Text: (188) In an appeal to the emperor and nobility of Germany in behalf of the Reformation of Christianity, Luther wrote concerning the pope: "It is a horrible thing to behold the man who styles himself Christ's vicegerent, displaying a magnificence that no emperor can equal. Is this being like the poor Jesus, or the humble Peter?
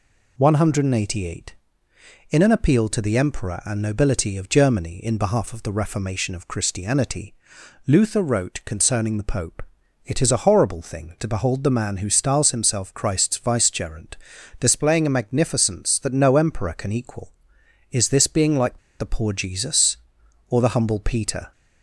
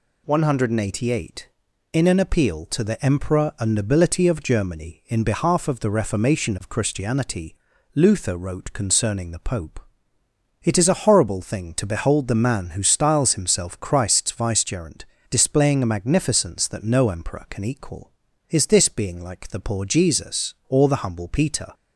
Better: second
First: pauses between "like" and "the"; slight; at 18.7 s; 0.22 s long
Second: none

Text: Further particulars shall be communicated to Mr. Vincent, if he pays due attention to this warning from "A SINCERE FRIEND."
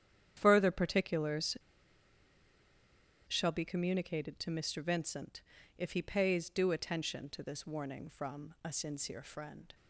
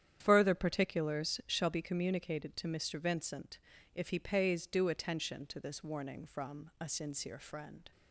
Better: second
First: starts louder than the rest; strong; until 1.3 s; 9.5 dB // pauses between "particulars" and "shall"; strong; at 1.5 s; 1.7 s long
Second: starts louder than the rest; strong; until 1.2 s; 9.5 dB

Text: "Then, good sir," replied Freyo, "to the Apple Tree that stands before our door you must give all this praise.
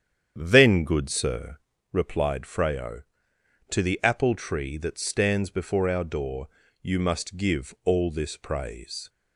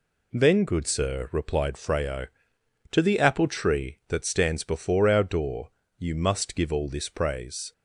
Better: second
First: starts louder than the rest; strong; until 1.9 s; 8.5 dB // pauses between "door" and "you"; slight; at 6.4 s; 0.36 s long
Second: pauses between "door" and "you"; slight; at 5.7 s; 0.26 s long

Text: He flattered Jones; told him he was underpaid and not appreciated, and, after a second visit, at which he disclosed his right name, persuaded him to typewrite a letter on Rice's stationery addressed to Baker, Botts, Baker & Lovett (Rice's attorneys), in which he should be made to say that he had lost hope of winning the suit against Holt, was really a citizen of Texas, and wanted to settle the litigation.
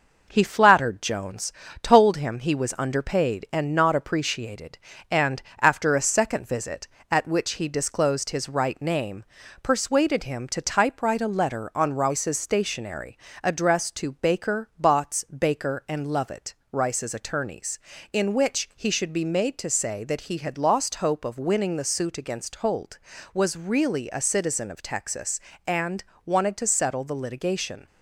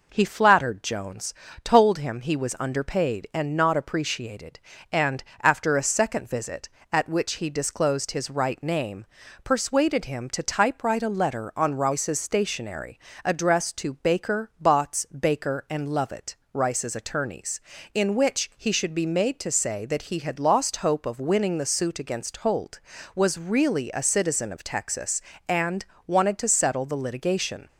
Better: second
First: gets quieter; slight; throughout; 3 dB // pauses between "stationery" and "addressed"; slight; at 13.1 s; 0.28 s long // pauses between "and" and "wanted"; slight; at 26.0 s; 0.24 s long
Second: pauses between "stationery" and "addressed"; slight; at 12.9 s; 0.28 s long // pauses between "and" and "wanted"; slight; at 25.8 s; 0.24 s long

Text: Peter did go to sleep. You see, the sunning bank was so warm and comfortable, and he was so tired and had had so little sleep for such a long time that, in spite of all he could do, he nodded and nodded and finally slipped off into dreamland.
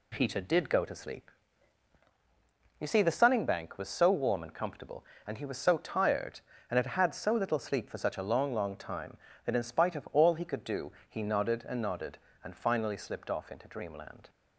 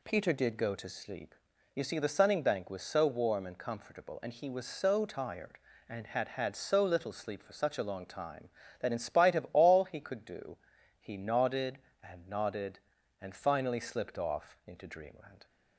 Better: second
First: says "long" twice; at 8.5 s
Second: none

